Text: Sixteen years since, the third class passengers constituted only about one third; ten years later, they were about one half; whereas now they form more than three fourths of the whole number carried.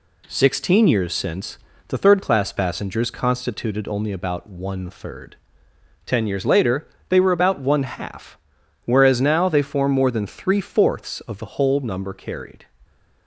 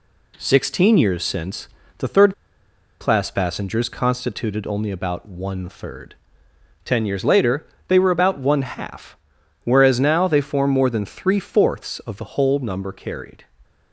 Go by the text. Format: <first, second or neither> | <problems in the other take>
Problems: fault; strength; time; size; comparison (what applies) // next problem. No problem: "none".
first | pauses between "third" and "class"; noticeable; at 2.3 s; 0.67 s long